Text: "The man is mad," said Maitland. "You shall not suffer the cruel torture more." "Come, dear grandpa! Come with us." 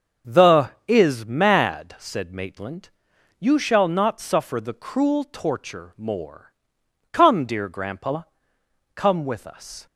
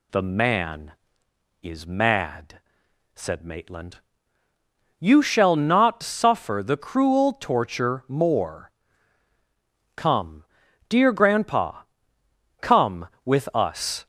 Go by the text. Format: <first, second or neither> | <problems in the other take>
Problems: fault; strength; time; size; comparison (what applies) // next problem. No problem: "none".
second | starts louder than the rest; until 1.4 s; 6.5 dB // skips "man"; at 0.7 s